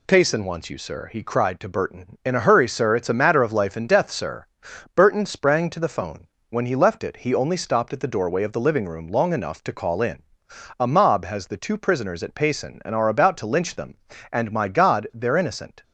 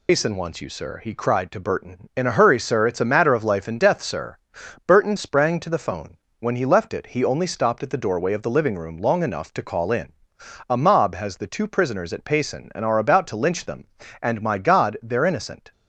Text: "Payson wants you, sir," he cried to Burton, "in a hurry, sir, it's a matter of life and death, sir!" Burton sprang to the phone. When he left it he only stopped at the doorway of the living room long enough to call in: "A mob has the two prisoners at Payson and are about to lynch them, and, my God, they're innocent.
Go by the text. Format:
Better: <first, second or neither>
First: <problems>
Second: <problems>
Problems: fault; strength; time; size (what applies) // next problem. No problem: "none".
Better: first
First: none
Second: loses the start of "Payson"; at 0.0 s; 110 ms